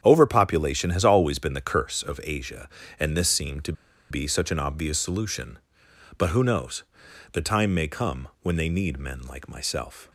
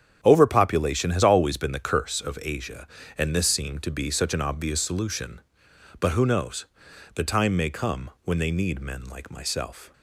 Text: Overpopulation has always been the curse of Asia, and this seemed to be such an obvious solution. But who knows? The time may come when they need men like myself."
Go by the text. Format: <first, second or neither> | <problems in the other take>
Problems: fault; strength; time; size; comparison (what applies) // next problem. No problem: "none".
second | starts louder than the rest; strong; until 1.0 s; 8.5 dB; strong in the second // pauses between "to" and "be"; at 3.7 s; 0.37 s long